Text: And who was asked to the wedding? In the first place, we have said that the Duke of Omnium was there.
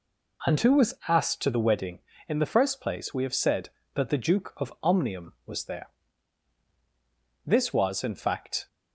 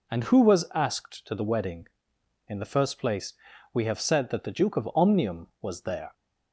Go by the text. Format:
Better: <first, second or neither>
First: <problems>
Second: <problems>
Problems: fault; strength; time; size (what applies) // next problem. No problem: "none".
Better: second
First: goes on to say "This was in fact"; noticeable; from 7.4 s on; 1.2 s long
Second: none